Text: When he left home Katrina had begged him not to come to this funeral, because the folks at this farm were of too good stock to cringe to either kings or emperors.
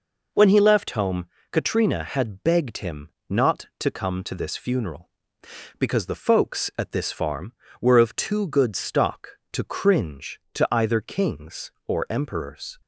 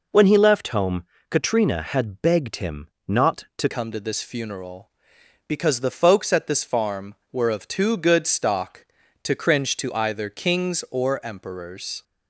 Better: first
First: pauses between "home" and "Katrina"; slight; at 1.2 s; 0.25 s long // pauses between "him" and "not"; slight; at 3.0 s; 0.20 s long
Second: pauses between "home" and "Katrina"; slight; at 1.0 s; 0.26 s long // pauses between "him" and "not"; slight; at 2.8 s; 0.20 s long // changes voice at "come"; from 3.7 s on; 8.3 s long

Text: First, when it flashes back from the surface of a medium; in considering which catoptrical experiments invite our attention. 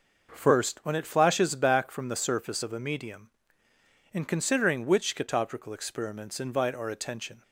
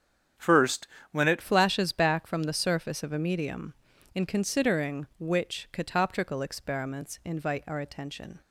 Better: first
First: none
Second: starts louder than the rest; strong; until 1.6 s; 8.5 dB // changes voice at "flashes"; from 1.4 s on; 7.0 s long

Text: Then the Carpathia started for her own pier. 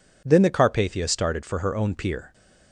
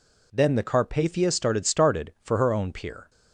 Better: first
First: none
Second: says "started" twice; at 1.6 s

